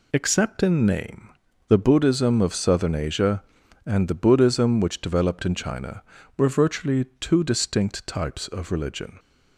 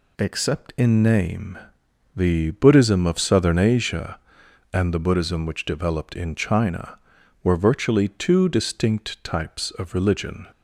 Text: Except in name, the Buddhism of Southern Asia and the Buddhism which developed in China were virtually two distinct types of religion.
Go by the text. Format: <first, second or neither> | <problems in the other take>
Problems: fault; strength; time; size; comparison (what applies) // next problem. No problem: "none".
neither | none